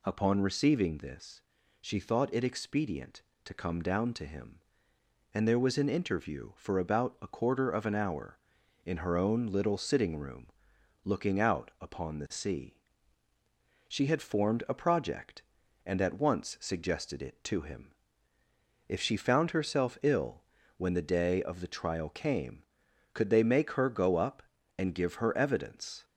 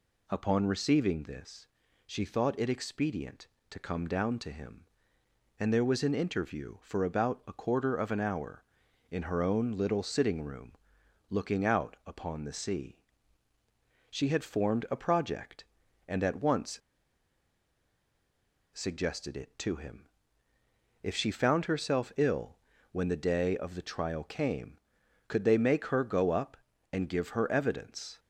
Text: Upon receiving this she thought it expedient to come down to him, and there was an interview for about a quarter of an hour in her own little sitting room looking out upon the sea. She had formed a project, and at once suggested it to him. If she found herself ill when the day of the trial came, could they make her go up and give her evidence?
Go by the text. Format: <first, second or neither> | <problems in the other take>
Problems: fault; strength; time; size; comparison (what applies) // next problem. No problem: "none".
first | pauses between "this" and "she"; at 1.6 s; 0.38 s long; also in the first // pauses between "room" and "looking"; noticeable; at 10.7 s; 0.58 s long; noticeable in the first // pauses between "once" and "suggested"; strong; at 16.8 s; 1.9 s long // pauses between "ill" and "when"; slight; at 22.5 s; 0.34 s long; slight in the first